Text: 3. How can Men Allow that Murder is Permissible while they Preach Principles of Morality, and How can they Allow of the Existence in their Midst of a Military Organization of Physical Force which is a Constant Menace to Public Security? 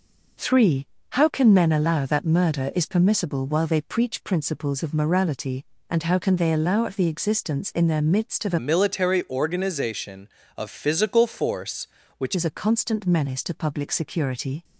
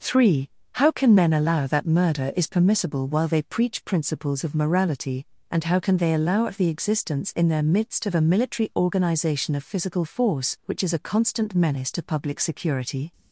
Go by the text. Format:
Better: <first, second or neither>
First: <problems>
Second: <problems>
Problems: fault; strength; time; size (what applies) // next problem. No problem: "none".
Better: second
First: changes voice from "Military" to "which"; from 8.5 to 12.3 s; 3.8 s long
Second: none